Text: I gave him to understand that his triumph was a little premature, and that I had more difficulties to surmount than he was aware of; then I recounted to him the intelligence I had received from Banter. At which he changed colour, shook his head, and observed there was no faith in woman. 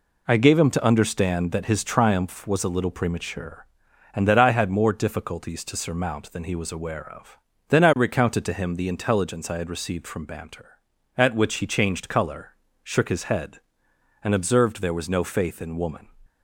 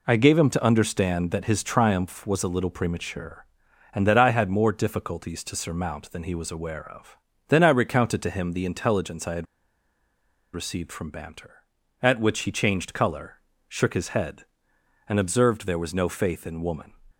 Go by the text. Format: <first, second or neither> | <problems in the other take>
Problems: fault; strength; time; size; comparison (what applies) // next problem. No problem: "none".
first | pauses between "had" and "received"; at 9.4 s; 1.0 s long